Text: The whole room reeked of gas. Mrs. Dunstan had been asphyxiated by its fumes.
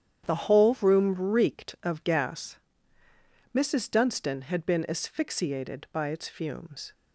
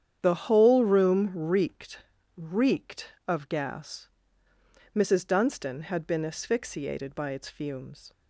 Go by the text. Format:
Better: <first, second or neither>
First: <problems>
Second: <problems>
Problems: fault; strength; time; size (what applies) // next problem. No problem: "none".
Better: first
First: starts louder than the rest; strong; until 1.3 s; 9.5 dB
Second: starts louder than the rest; strong; until 1.2 s; 9 dB // says "reeked" twice; at 2.3 s